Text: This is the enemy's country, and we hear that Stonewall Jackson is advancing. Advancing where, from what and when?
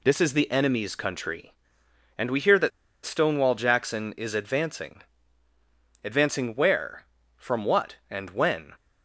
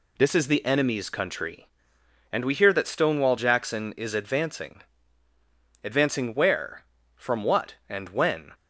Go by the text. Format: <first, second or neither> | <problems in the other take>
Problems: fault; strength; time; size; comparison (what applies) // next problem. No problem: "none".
second | pauses between "that" and "Stonewall"; slight; at 2.7 s; 0.35 s long